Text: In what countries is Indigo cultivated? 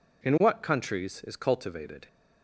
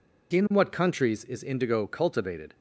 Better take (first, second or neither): second